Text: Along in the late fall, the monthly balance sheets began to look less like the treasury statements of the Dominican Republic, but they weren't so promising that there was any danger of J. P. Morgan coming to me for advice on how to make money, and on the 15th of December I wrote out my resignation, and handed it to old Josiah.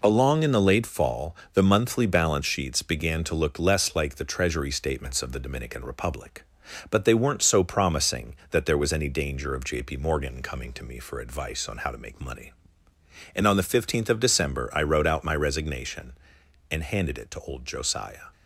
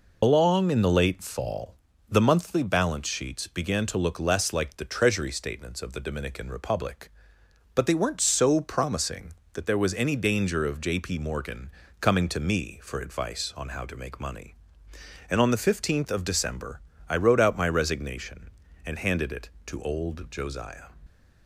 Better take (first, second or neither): first